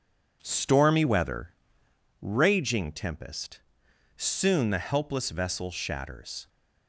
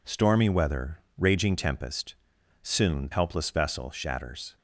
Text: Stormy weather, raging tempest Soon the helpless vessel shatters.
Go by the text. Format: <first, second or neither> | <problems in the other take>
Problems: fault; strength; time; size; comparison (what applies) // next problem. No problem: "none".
first | pauses between "tempest" and "Soon"; noticeable; at 2.1 s; 0.48 s long; noticeable in the first // skips "the"; at 3.1 s